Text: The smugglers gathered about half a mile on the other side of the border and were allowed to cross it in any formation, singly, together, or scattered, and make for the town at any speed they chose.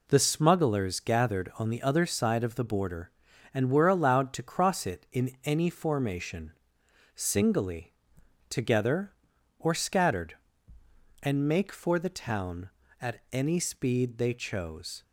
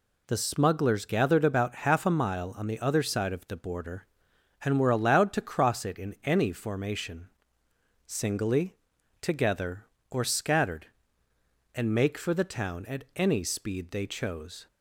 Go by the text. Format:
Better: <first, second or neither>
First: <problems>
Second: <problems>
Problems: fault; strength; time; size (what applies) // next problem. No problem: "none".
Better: second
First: skips "about half a mile"; at 1.5 s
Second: none